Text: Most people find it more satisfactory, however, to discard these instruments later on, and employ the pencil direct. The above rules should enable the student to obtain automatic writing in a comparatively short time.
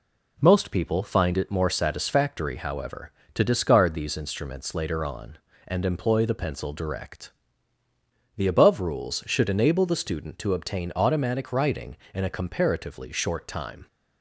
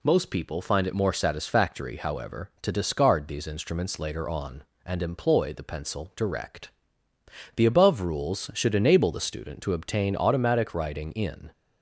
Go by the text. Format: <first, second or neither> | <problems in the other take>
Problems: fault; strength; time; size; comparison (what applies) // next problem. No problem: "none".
first | stops before "a comparatively short time"; at 11.5 s